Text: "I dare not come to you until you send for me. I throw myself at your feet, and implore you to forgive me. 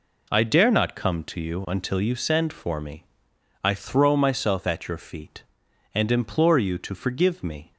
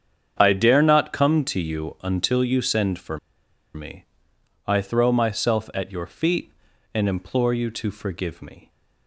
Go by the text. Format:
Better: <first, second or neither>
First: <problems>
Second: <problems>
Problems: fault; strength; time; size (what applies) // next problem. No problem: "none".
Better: first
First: none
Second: starts louder than the rest; strong; until 1.4 s; 7.5 dB // pauses between "for" and "me"; noticeable; at 3.1 s; 0.57 s long